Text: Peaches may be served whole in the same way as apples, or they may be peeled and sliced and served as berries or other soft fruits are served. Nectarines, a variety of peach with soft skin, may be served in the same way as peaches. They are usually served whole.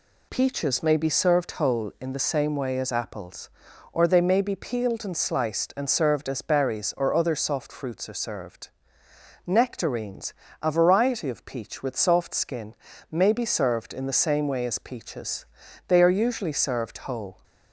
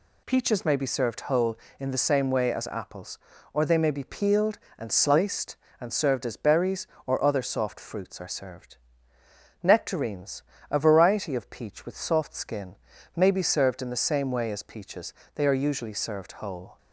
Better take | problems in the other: neither | none

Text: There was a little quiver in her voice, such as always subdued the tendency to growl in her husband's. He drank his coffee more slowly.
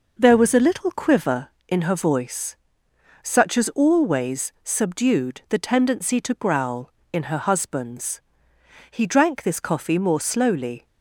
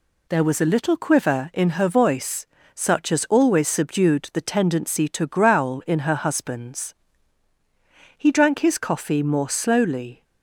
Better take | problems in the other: second | says "this" for "his"; at 9.4 s

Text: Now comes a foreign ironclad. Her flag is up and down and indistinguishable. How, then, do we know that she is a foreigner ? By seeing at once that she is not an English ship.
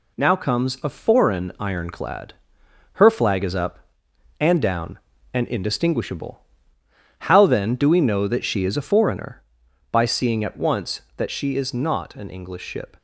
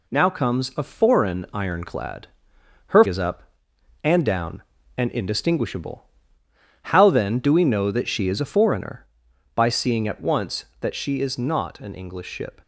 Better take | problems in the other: first | skips "flag"; at 3.0 s

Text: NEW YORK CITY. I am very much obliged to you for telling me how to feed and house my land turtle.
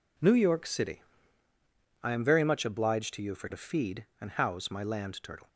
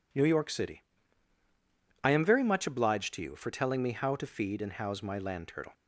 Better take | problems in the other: second | skips "telling me how"; at 3.4 s

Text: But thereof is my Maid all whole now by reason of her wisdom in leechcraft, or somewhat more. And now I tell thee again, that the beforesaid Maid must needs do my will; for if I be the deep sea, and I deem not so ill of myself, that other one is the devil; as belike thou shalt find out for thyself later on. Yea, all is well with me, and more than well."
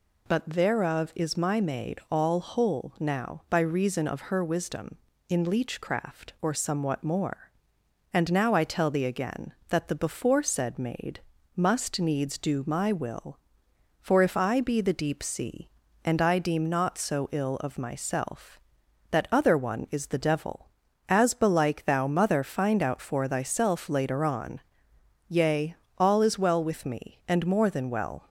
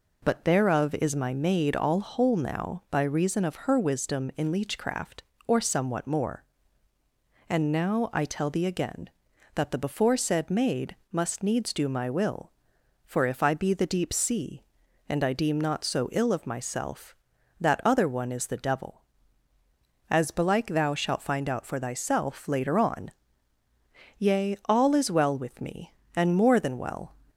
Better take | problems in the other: second | pauses between "Maid" and "must"; at 11.1 s; 0.38 s long; slight in the second // says "mother" for "shalt"; at 22.0 s

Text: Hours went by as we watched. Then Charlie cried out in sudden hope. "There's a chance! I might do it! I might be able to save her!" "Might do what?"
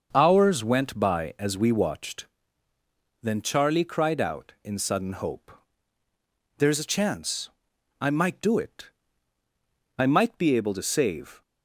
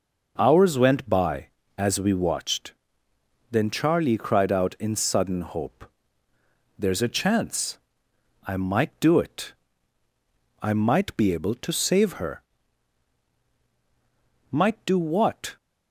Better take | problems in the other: second | starts louder than the rest; until 1.1 s; 6.5 dB // stops before "her Might do what"; at 11.4 s

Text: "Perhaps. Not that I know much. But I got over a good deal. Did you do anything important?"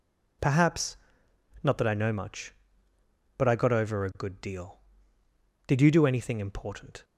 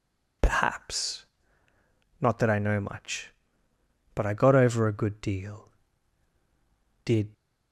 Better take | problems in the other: first | stops before "you do anything important"; at 7.3 s

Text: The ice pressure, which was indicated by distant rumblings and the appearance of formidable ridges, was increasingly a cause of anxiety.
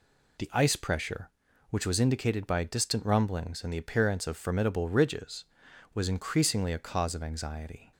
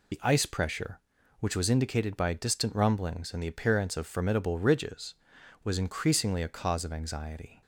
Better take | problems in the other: first | loses the start of "The"; at 0.1 s; 25 ms

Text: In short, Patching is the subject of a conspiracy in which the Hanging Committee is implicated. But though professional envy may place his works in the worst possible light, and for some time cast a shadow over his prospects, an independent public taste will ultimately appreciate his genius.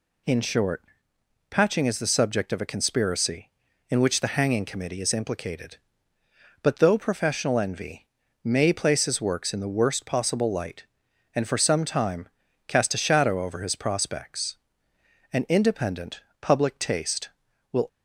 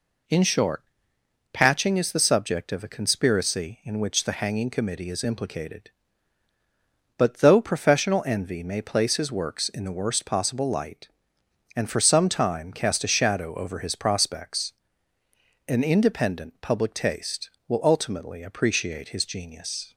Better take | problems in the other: second | pauses between "envy" and "may"; slight; at 8.0 s; 0.36 s long // pauses between "time" and "cast"; at 12.2 s; 0.38 s long // pauses between "independent" and "public"; slight; at 16.2 s; 0.20 s long // stops before "ultimately appreciate his genius"; at 17.8 s

